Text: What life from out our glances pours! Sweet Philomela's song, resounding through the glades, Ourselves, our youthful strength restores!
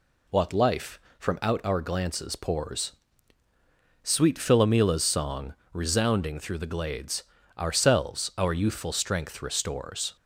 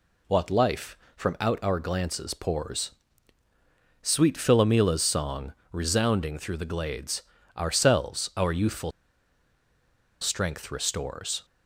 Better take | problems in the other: first | pauses between "youthful" and "strength"; strong; at 8.9 s; 1.3 s long

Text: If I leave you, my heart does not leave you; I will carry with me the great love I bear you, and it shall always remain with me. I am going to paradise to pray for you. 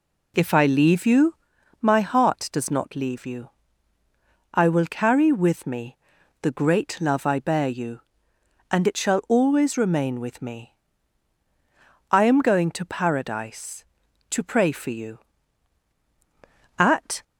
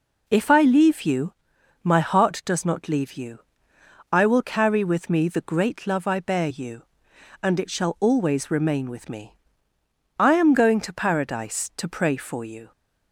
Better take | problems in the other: second | pauses between "me" and "the"; noticeable; at 5.9 s; 0.46 s long // goes on to say "At"; slight; from 16.7 s on; 0.44 s long

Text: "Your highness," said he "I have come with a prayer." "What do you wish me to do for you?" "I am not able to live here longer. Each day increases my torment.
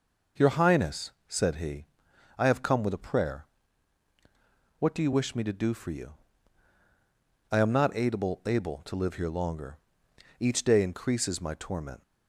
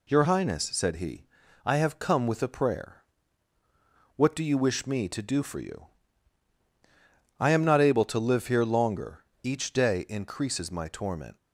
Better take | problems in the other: second | pauses between "he" and "I"; noticeable; at 1.8 s; 0.50 s long; also in the second // says "able" twice; at 8.4 s

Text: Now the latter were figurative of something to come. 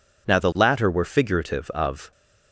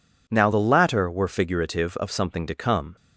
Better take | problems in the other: second | stops before "something to come"; at 2.1 s

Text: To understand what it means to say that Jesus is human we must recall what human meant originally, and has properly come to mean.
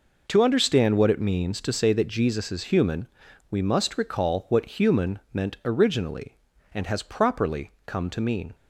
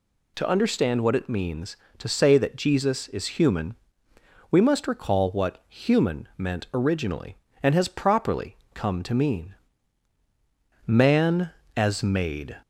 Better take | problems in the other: first | pauses between "human" and "we"; noticeable; at 3.7 s; 0.76 s long; also in the first // pauses between "properly" and "come"; slight; at 8.5 s; 0.16 s long; slight in the first // goes on to say "Man as made"; strong; from 10.8 s on; 1.7 s long

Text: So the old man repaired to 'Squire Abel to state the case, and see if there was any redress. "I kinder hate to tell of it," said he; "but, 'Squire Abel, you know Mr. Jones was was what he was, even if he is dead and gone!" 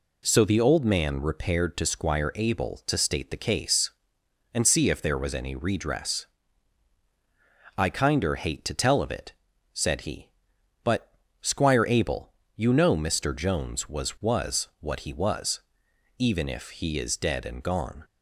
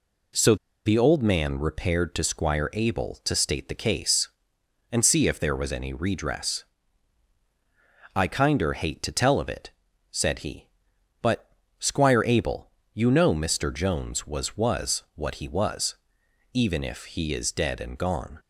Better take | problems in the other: first | pauses between "So" and "the"; slight; at 0.5 s; 0.29 s long

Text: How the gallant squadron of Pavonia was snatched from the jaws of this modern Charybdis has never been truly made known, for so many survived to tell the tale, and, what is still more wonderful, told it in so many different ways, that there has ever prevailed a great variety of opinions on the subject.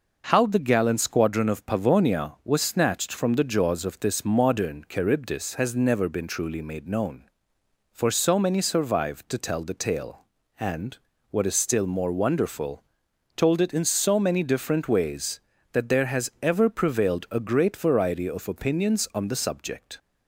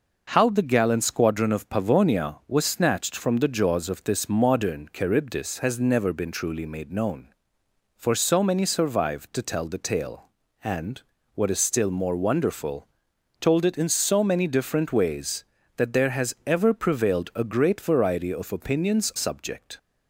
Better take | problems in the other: first | skips "on the"; at 19.1 s

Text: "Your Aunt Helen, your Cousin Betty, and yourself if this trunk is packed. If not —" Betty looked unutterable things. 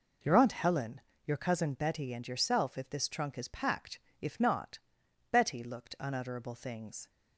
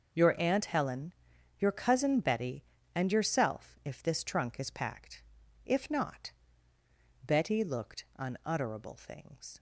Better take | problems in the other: neither | none

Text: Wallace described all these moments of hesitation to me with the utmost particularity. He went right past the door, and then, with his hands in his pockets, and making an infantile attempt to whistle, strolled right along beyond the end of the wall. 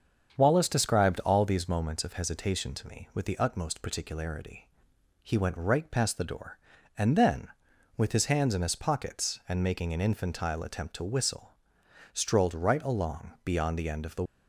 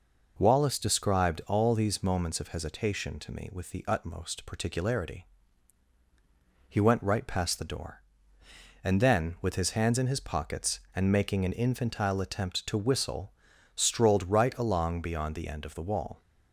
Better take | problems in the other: second | starts louder than the rest; strong; until 1.3 s; 7.5 dB // stops before "wall"; at 14.2 s

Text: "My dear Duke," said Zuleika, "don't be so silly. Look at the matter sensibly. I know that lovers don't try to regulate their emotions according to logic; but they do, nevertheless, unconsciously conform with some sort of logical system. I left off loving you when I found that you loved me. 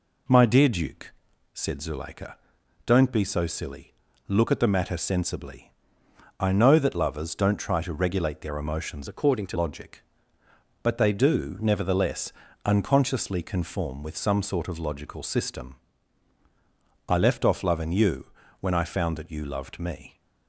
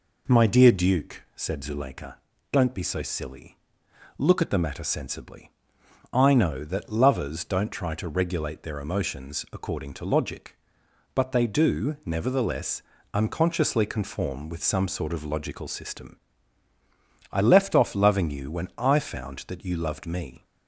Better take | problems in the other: second | changes voice from "according" to "to"; from 9.0 to 9.5 s; 0.5 s long // pauses between "you" and "when"; slight; at 18.2 s; 0.34 s long

